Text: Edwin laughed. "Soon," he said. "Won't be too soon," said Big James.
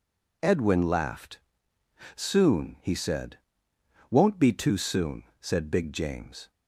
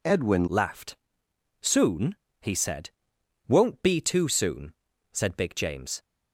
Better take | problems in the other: first | changes voice at "laughed"; from 0.4 s on; 5.6 s long

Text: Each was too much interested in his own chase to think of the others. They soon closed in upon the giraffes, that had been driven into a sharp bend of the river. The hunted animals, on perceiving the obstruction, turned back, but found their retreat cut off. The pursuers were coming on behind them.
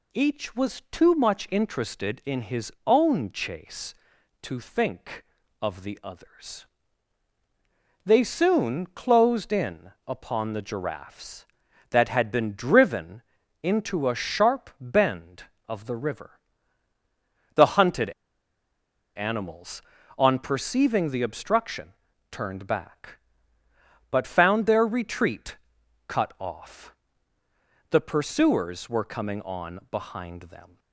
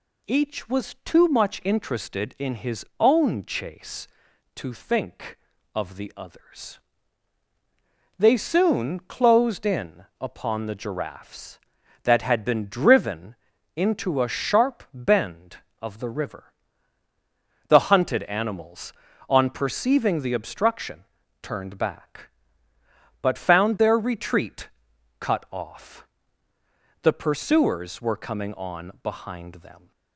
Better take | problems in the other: second | pauses between "driven" and "into"; at 13.2 s; 0.40 s long; also in the second // pauses between "hunted" and "animals"; at 18.1 s; 1.0 s long // pauses between "retreat" and "cut"; noticeable; at 25.5 s; 0.54 s long; noticeable in the second

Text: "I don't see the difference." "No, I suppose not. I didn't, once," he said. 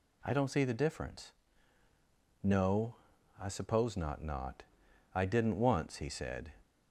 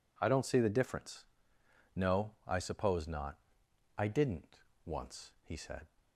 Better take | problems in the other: second | says "not" twice; at 4.2 s

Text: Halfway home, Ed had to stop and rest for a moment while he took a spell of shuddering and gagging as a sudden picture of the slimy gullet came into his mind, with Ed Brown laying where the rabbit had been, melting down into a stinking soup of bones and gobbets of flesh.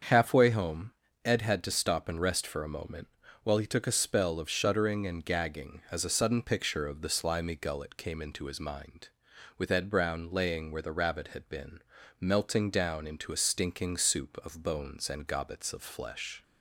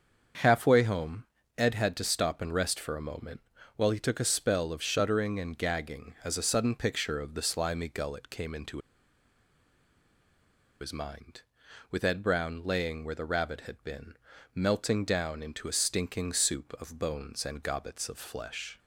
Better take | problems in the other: first | starts louder than the rest; until 1.7 s; 7 dB; also in the first // pauses between "moment" and "while"; at 3.3 s; 0.38 s long; also in the first // pauses between "into" and "his"; strong; at 8.7 s; 2.0 s long

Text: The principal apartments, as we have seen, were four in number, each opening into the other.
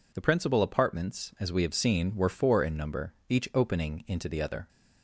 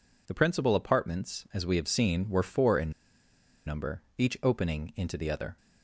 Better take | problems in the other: first | pauses between "in" and "number"; noticeable; at 2.9 s; 0.75 s long

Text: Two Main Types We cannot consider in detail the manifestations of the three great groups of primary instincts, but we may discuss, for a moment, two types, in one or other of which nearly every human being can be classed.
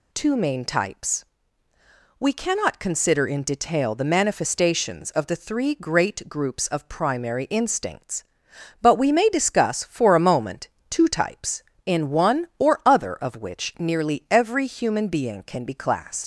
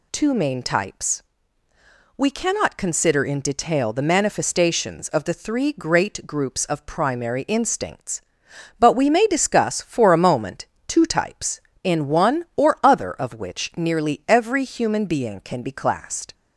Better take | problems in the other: second | pauses between "Types" and "We"; noticeable; at 1.2 s; 0.96 s long; noticeable in the second // leaves "classed" unfinished; at 16.2 s; 90 ms

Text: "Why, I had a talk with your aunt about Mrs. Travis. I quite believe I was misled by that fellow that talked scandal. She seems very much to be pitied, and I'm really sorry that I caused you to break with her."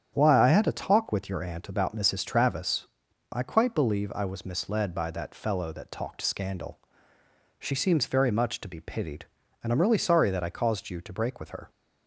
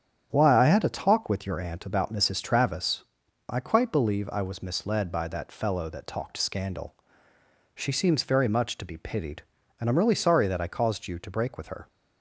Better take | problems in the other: neither | starts louder than the rest; strong; the same in both

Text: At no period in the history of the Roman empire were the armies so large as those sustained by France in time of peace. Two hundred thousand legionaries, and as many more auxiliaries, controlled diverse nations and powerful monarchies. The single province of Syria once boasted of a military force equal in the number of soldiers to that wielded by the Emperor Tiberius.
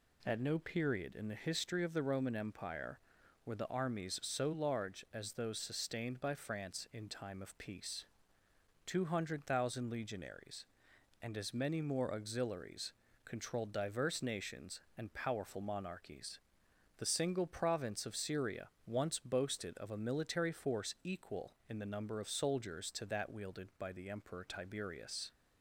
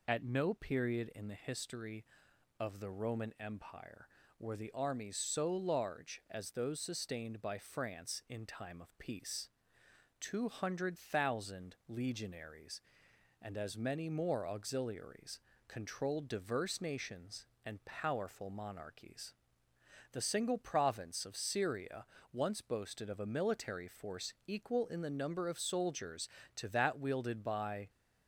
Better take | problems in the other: first | pauses between "Syria" and "once"; slight; at 22.0 s; 0.26 s long; slight in the first // stops before "the Emperor Tiberius"; at 27.8 s

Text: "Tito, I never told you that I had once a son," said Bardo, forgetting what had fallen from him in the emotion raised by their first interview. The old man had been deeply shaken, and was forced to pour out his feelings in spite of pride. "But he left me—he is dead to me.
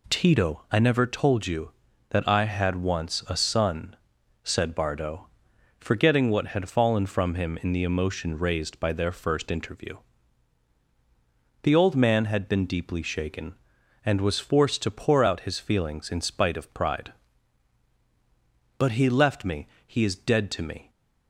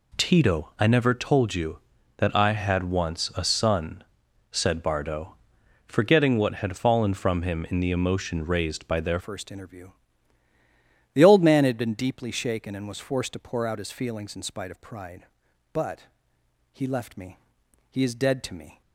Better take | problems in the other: first | changes voice at "first"; from 9.1 s on; 9.7 s long // pauses between "But" and "he"; noticeable; at 16.0 s; 0.68 s long

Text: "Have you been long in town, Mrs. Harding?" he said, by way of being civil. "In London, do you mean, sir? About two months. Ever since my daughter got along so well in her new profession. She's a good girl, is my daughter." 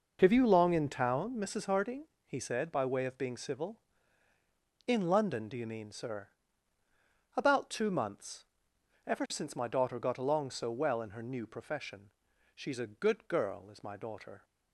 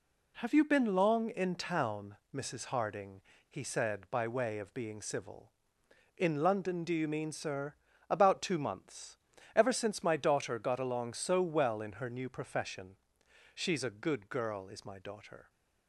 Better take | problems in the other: second | skips "been"; at 0.4 s

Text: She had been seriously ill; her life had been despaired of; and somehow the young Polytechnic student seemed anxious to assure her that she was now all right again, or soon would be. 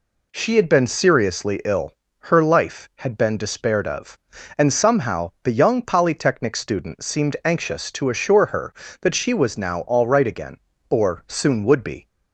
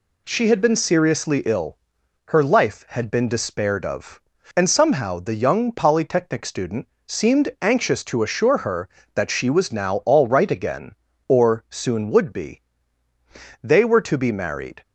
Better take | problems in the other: first | pauses between "student" and "seemed"; slight; at 6.8 s; 0.18 s long // goes on to say "They were to be married"; noticeable; from 13.6 s on; 1.2 s long

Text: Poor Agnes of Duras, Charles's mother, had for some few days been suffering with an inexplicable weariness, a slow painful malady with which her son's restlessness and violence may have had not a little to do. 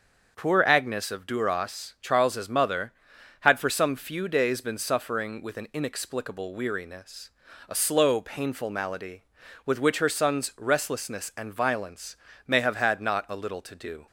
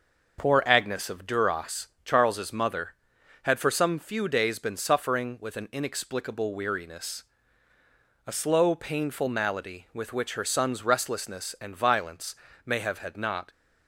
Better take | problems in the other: first | starts louder than the rest; noticeable; until 1.4 s; 6 dB; also in the first // pauses between "violence" and "may"; slight; at 12.3 s; 0.28 s long; slight in the first // stops before "a little to do"; at 13.5 s

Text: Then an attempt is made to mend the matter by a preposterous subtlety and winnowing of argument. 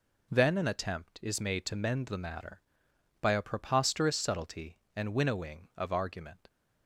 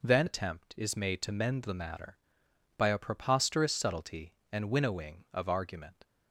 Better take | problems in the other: first | skips "an"; at 0.2 s

